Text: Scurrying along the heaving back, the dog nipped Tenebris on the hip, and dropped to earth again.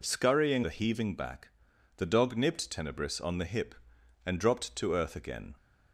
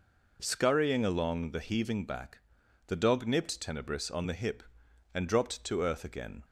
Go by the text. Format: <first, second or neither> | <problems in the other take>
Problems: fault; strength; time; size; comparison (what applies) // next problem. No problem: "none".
second | skips "along"; at 0.6 s